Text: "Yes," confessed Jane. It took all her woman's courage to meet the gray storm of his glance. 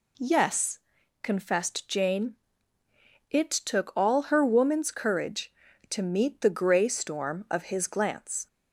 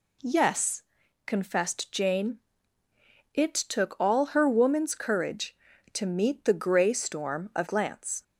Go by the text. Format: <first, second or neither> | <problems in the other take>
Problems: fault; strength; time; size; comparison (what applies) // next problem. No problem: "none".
first | skips "his"; at 7.6 s